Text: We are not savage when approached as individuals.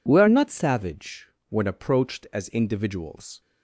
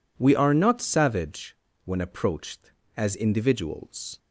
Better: neither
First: pauses between "savage" and "when"; slight; at 1.2 s; 0.20 s long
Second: pauses between "savage" and "when"; slight; at 1.5 s; 0.28 s long

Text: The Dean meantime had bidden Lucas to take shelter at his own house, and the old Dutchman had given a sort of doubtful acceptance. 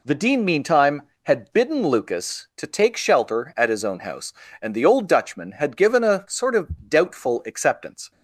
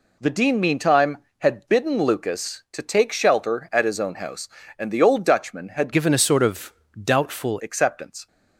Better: first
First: none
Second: changes voice from "given" to "doubtful"; from 5.9 to 7.5 s; 1.6 s long // pauses between "of" and "doubtful"; slight; at 6.7 s; 0.30 s long

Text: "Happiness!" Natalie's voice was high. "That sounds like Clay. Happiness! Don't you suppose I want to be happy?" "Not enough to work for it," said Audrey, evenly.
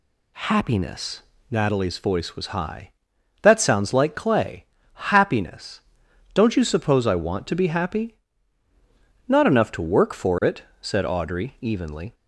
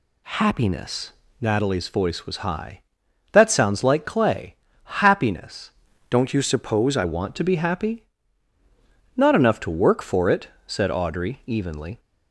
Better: first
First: none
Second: changes voice from "Don't" to "I"; from 6.0 to 7.0 s; 1.0 s long

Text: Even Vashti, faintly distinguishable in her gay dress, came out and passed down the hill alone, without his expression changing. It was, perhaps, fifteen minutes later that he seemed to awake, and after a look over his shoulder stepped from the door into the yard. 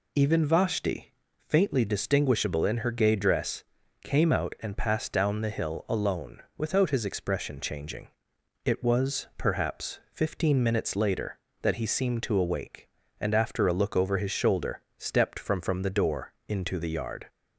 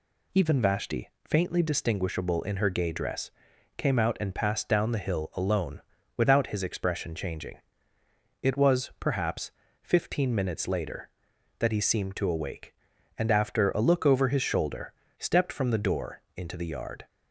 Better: second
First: pauses between "shoulder" and "stepped"; slight; at 14.8 s; 0.16 s long // says "from" twice; at 15.6 s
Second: pauses between "shoulder" and "stepped"; slight; at 14.9 s; 0.26 s long

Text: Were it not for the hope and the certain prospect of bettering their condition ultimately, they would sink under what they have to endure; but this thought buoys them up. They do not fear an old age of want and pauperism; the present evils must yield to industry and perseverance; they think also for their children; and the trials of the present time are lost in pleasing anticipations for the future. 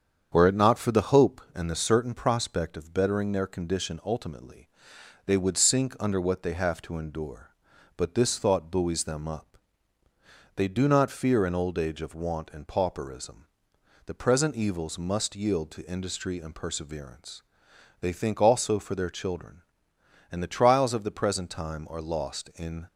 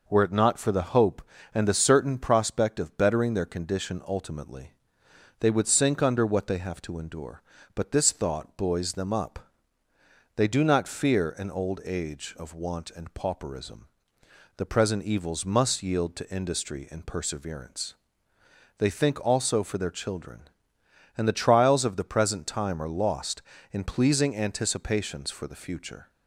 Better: second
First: starts louder than the rest; strong; until 1.3 s; 8 dB // stops before "pleasing anticipations for the future"; at 22.8 s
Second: none

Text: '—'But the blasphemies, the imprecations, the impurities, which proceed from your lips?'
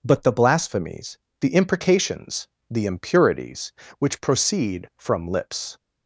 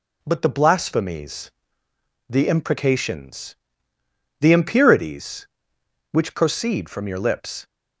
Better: second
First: skips "your"; at 5.2 s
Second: none

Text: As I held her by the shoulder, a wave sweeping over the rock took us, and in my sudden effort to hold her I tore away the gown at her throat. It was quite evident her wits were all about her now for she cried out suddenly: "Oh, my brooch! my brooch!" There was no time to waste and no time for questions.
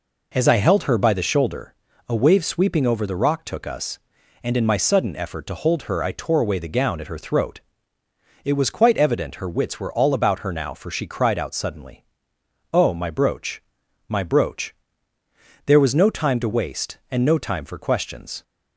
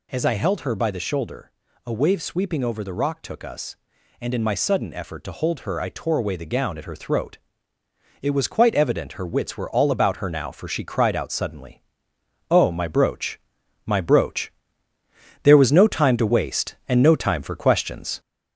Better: first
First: none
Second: gets louder; noticeable; throughout; 4 dB

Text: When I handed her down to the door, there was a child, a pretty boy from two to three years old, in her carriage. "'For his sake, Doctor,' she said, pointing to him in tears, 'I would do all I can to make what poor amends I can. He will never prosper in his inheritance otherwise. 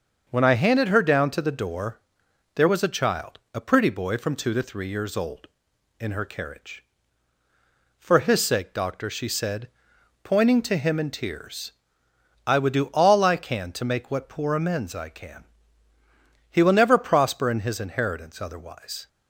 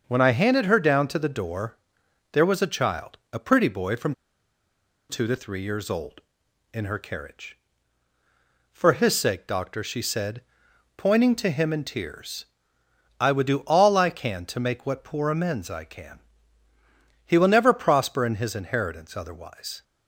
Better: first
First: starts louder than the rest; until 1.2 s; 6.5 dB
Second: starts louder than the rest; until 1.0 s; 6.5 dB // pauses between "from" and "two"; noticeable; at 4.1 s; 0.95 s long

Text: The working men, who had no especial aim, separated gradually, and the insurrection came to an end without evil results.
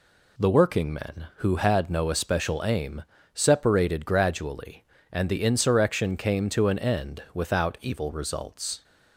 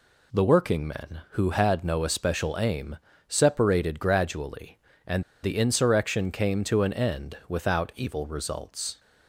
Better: first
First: none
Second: pauses between "and" and "the"; slight; at 5.2 s; 0.20 s long

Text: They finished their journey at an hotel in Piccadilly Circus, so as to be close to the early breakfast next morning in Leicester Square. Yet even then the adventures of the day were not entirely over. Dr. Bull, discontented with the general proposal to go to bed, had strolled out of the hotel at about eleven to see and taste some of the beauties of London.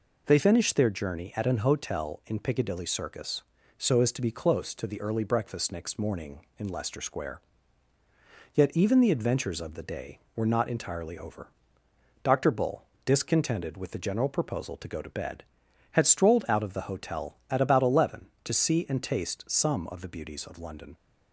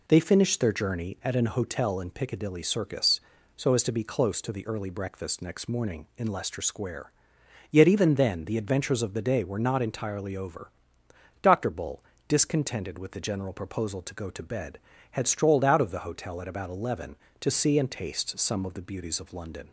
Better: second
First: skips "then"; at 9.0 s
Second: none

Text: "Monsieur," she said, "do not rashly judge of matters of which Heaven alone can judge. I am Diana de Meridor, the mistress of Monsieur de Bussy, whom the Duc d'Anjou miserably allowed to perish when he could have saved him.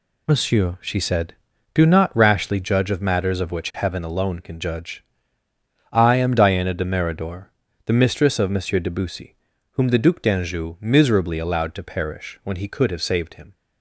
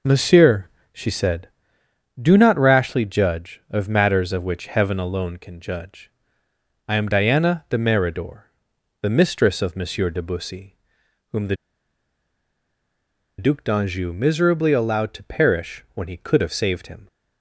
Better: first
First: none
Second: pauses between "the" and "Duc"; strong; at 11.5 s; 1.8 s long

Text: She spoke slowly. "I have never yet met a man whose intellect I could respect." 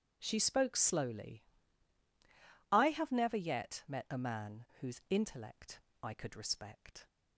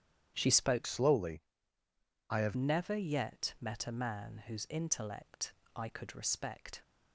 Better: first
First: starts louder than the rest; strong; until 1.2 s; 8.5 dB // pauses between "intellect" and "I"; slight; at 5.8 s; 0.22 s long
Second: starts louder than the rest; strong; until 1.3 s; 10 dB // changes voice from "slowly" to "have"; from 0.8 to 2.5 s; 1.7 s long // pauses between "intellect" and "I"; slight; at 5.5 s; 0.24 s long

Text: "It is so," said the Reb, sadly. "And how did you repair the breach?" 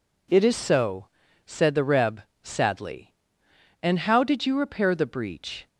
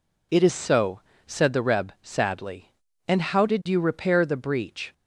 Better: neither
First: none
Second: none

